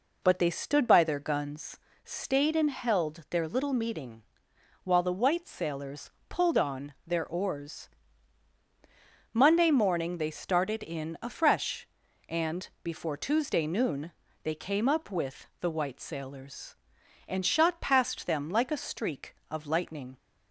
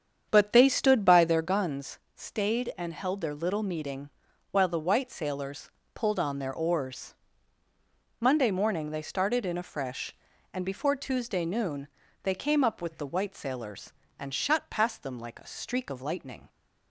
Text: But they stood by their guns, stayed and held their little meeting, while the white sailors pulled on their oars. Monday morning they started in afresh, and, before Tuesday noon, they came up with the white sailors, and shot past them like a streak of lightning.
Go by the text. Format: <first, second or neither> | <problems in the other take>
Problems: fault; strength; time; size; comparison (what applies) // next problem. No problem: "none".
first | starts louder than the rest; strong; until 1.5 s; 8 dB // pauses between "sailors" and "pulled"; slight; at 5.7 s; 0.24 s long; slight in the first